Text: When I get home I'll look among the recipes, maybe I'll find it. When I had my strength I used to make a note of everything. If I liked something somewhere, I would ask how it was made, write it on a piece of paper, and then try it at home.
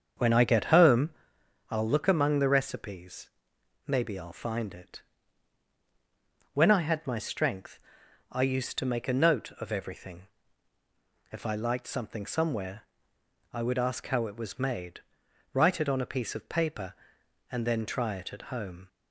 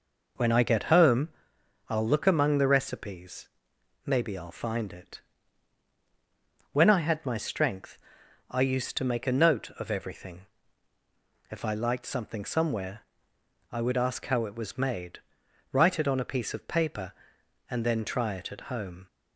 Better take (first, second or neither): second